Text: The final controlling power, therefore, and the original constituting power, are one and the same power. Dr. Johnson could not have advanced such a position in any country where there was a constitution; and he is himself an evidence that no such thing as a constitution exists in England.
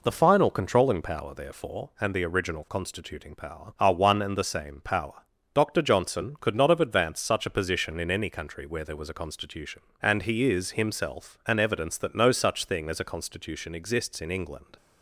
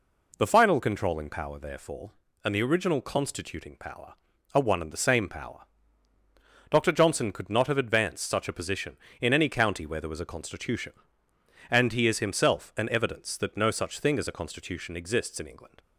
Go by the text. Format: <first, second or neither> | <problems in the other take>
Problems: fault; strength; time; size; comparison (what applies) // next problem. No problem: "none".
first | says "county" for "country"; at 9.4 s